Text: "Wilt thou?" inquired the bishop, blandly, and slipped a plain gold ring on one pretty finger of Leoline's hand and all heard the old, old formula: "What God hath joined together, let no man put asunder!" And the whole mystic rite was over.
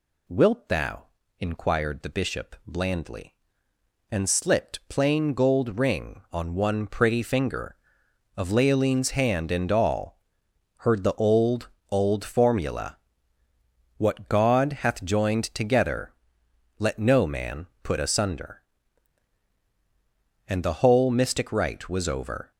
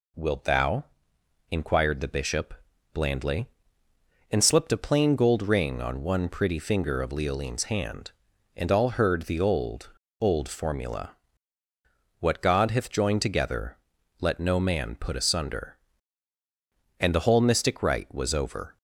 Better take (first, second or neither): second